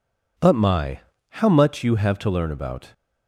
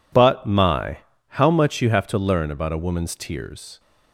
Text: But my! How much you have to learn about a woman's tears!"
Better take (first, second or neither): second